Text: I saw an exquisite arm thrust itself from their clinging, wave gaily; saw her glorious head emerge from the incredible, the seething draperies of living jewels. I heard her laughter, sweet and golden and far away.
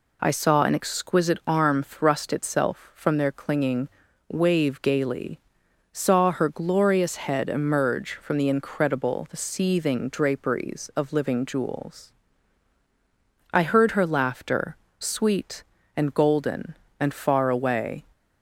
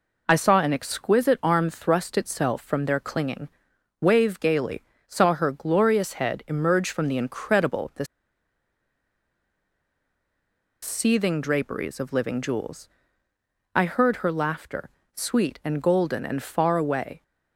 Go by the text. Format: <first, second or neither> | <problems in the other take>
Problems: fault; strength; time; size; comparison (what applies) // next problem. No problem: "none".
first | pauses between "the" and "seething"; strong; at 8.0 s; 2.7 s long